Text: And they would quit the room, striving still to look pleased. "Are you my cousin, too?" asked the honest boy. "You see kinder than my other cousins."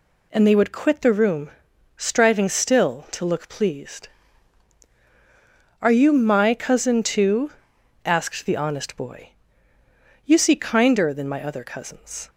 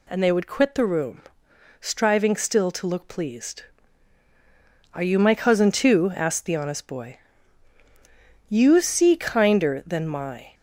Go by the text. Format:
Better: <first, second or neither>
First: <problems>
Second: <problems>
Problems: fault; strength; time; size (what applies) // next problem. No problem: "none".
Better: first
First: none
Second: stops before "other cousins"; at 10.5 s